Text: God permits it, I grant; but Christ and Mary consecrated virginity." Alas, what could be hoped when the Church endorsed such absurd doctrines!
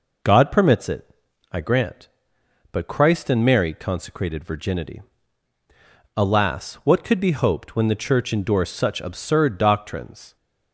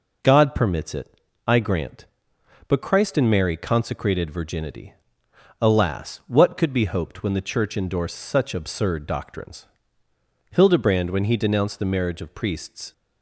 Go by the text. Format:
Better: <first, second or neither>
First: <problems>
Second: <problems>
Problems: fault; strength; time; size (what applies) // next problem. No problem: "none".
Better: first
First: none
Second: goes on to say "Hildebrand when he denounced the marriage of priests"; strong; from 10.5 s on; 2.4 s long